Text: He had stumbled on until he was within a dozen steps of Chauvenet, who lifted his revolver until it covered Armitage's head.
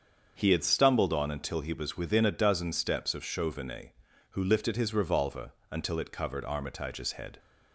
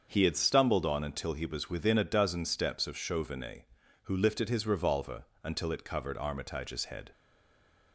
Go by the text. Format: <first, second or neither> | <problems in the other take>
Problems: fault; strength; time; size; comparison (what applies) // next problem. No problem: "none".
first | starts louder than the rest; until 1.1 s; 7 dB; also in the first // pauses between "revolver" and "until"; slight; at 5.2 s; 0.18 s long; slight in the first // stays silent after the last word; slight; from 7.1 s on; 0.8 s long